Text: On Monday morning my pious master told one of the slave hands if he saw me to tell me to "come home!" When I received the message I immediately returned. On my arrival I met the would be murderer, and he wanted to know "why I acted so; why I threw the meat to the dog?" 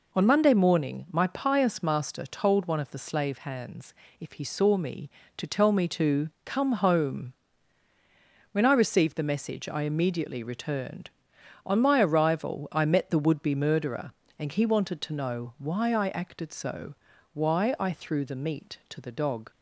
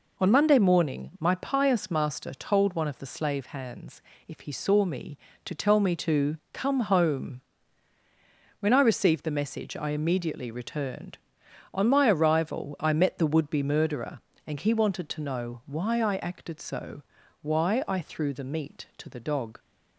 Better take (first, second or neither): neither